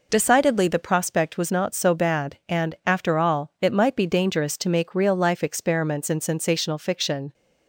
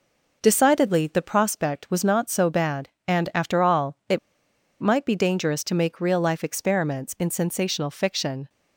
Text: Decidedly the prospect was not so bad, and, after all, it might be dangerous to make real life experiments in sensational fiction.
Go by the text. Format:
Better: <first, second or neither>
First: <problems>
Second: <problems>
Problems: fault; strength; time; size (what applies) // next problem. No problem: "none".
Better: first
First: none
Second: pauses between "it" and "might"; noticeable; at 4.1 s; 0.62 s long